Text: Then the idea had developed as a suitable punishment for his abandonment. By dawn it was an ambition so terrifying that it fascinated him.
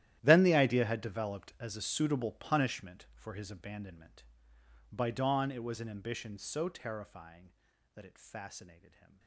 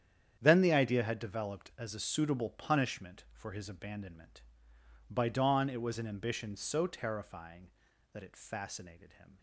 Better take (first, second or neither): second